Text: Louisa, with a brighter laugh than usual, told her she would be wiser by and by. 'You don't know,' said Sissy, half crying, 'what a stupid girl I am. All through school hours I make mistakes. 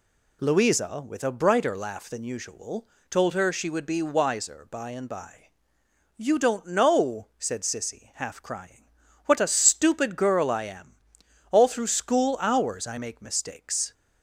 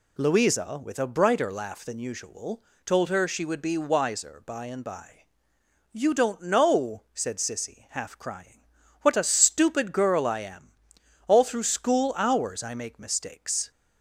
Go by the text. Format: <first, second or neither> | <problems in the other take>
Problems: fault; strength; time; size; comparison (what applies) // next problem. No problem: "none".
neither | none